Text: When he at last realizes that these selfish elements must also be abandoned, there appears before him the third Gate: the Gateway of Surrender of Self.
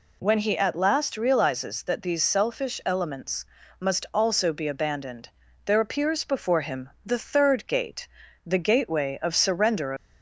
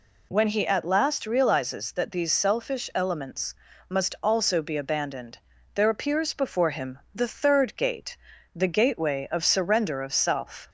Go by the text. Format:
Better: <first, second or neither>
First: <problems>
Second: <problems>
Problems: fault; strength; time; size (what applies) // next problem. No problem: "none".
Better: second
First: pauses between "elements" and "must"; slight; at 3.4 s; 0.34 s long // pauses between "him" and "the"; slight; at 6.8 s; 0.16 s long // stops before "of Self"; at 9.9 s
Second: pauses between "elements" and "must"; slight; at 3.5 s; 0.34 s long // pauses between "him" and "the"; slight; at 6.9 s; 0.16 s long